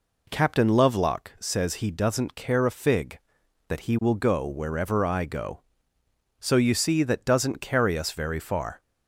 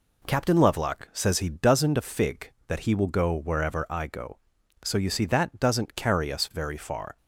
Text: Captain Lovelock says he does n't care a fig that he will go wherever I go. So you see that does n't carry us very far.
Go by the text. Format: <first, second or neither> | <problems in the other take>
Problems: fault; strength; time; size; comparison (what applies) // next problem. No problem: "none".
first | skips "care"; at 1.9 s